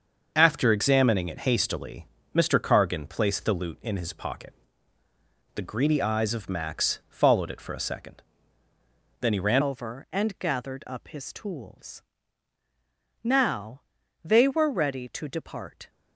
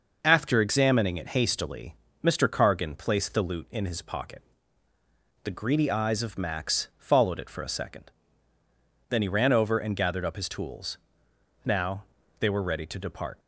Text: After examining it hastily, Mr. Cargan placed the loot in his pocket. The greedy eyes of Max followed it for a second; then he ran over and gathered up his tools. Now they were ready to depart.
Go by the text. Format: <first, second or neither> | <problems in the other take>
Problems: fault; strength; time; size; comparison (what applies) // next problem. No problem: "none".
second | starts louder than the rest; until 1.3 s; 6.5 dB // changes voice at "over"; from 9.6 s on; 6.2 s long // pauses between "Now" and "they"; at 13.8 s; 0.42 s long; slight in the second